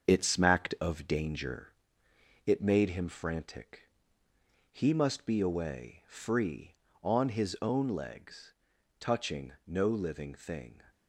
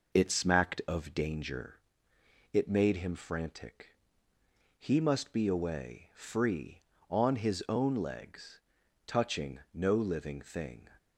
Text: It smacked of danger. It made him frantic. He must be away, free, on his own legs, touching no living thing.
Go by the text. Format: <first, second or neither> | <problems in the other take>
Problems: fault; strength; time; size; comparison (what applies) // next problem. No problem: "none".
second | gets quieter; throughout; 6 dB